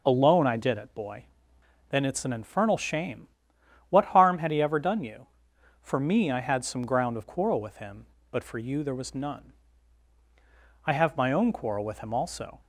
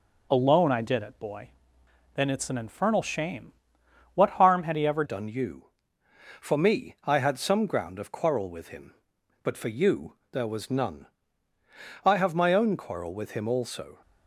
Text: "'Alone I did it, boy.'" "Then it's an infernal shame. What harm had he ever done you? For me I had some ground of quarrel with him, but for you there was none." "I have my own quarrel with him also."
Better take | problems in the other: first | changes voice at "done"; from 5.0 s on; 8.9 s long // pauses between "you" and "there"; slight; at 10.1 s; 0.16 s long

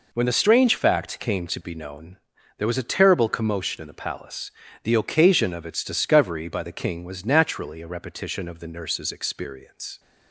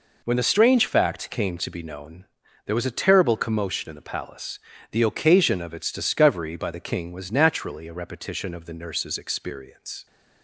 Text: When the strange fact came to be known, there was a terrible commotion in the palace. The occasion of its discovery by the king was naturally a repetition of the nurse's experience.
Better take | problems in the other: neither | none

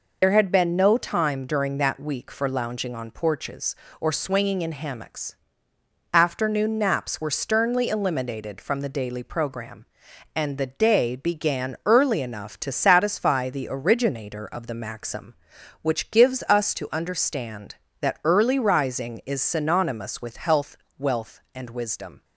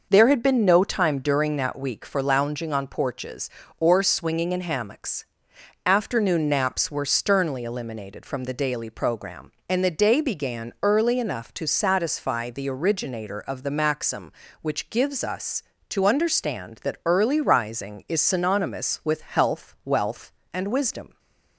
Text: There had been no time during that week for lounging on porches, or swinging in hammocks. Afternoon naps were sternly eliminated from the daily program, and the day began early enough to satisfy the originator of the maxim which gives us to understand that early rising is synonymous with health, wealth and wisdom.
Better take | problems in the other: second | loses the start of "There"; at 0.2 s; 65 ms

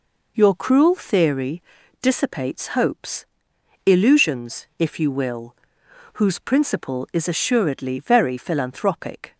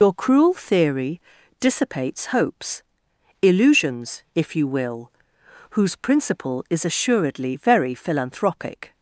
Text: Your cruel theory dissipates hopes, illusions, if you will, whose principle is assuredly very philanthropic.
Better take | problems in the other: first | loses the start of "Your"; at 0.0 s; 60 ms // pauses between "theory" and "dissipates"; at 1.2 s; 0.38 s long; also in the first

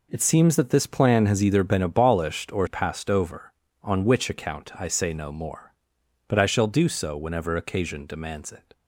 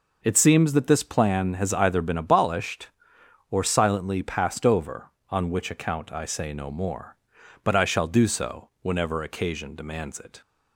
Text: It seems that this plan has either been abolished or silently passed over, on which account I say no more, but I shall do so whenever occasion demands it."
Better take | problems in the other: second | skips "silently"; at 2.6 s

